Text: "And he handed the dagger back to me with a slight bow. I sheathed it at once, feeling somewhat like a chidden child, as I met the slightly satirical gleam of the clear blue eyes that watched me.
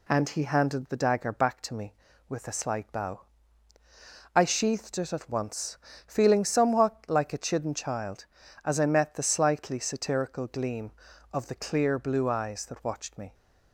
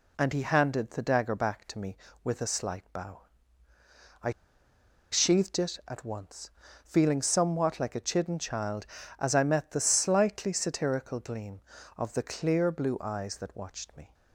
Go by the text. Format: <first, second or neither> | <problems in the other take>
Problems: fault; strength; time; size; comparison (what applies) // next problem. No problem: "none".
first | pauses between "I" and "sheathed"; noticeable; at 4.3 s; 0.81 s long